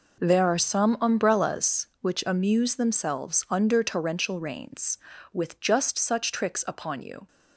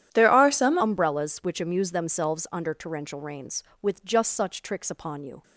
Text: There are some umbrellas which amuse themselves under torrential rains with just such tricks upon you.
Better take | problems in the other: first | changes voice at "umbrellas"; from 0.8 s on; 4.6 s long

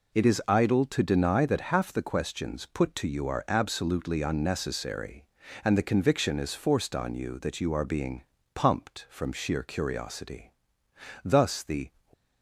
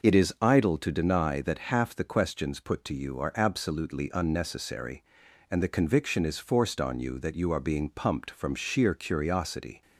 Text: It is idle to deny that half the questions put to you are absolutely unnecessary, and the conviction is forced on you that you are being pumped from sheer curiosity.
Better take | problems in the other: second | pauses between "being" and "pumped"; slight; at 8.2 s; 0.30 s long // goes on to say "Thus the"; noticeable; from 11.2 s on; 0.66 s long

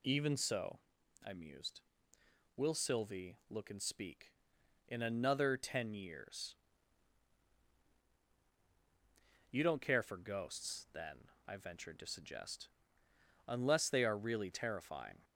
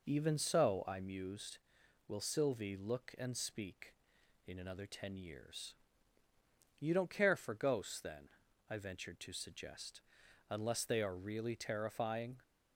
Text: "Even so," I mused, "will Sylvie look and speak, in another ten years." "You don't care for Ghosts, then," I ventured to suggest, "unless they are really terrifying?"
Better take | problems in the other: neither | none

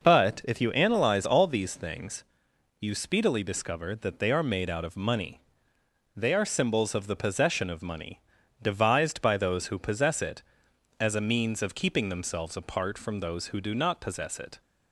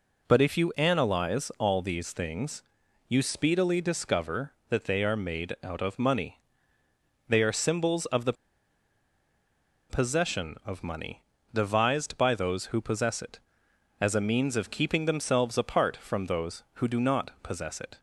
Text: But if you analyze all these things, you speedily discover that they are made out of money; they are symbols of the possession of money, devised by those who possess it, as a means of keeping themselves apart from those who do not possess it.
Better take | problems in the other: first | pauses between "the" and "possession"; strong; at 8.3 s; 1.5 s long

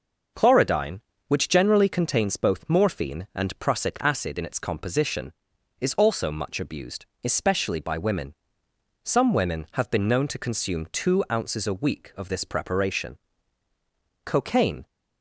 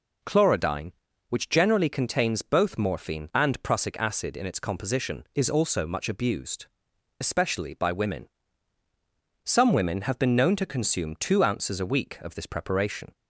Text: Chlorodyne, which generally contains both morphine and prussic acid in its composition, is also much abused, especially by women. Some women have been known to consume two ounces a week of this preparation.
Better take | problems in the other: second | goes on to say "Cocaine"; from 14.2 s on; 0.60 s long

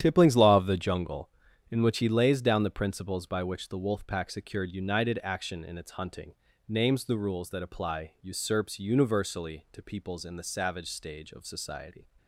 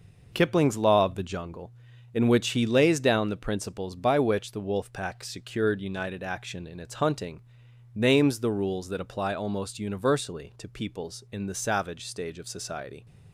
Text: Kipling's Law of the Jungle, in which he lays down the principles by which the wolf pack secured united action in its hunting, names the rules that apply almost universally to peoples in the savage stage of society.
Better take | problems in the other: second | starts louder than the rest; strong; until 1.0 s; 10.5 dB // says "usurps" for "almost"; at 8.2 s

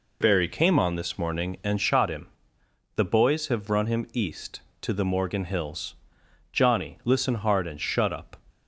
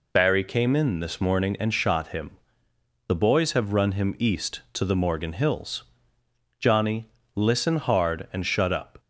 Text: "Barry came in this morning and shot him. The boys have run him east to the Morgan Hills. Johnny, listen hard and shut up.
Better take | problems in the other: second | says "on" for "in"; at 0.7 s

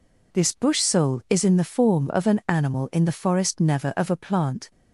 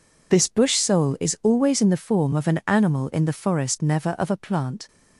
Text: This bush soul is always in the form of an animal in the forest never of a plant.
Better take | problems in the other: second | skips "always"; at 1.4 s

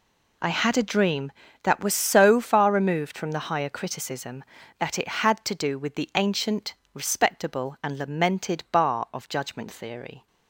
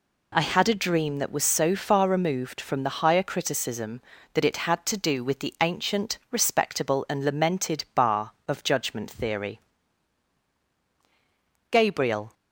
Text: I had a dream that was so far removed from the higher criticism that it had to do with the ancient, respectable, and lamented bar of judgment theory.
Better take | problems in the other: first | goes on to say "Gabriel"; noticeable; from 11.6 s on; 0.64 s long

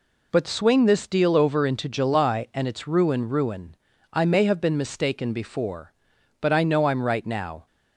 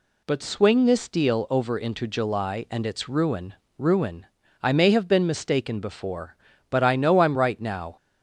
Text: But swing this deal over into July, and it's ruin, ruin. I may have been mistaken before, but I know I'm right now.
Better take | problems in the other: neither | none

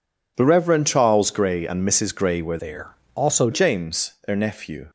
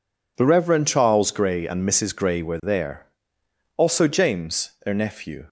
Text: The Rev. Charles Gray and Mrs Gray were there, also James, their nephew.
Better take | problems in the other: second | changes voice from "there" to "also"; from 2.5 to 3.4 s; 0.9 s long

